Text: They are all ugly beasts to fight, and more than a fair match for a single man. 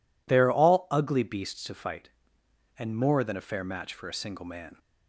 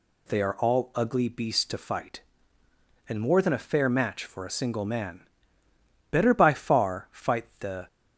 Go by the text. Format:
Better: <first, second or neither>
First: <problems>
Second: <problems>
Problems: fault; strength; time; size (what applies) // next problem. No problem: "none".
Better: first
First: none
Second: goes on to say "Better by far fight the"; strong; from 6.1 s on; 1.7 s long